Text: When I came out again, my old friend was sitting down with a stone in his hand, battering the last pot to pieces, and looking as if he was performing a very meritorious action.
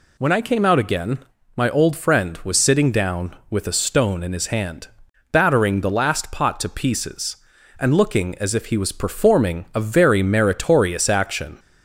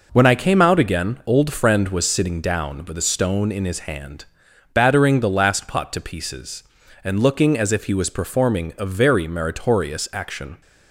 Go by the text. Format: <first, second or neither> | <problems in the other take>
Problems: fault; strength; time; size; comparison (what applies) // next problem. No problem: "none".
first | skips "my"; at 1.2 s